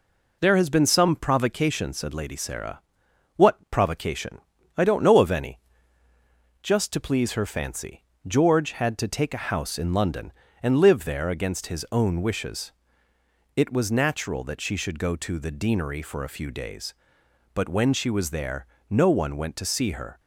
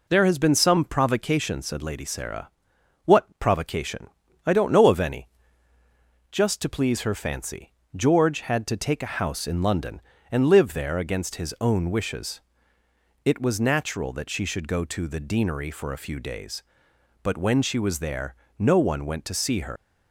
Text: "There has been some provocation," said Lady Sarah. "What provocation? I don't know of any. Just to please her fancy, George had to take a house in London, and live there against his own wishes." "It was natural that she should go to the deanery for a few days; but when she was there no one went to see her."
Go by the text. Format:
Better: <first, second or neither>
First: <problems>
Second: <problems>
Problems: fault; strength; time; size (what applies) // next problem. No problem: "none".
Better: first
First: pauses between "there" and "no"; slight; at 18.6 s; 0.24 s long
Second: pauses between "there" and "no"; slight; at 18.3 s; 0.24 s long // leaves "her" unfinished; at 19.7 s; 125 ms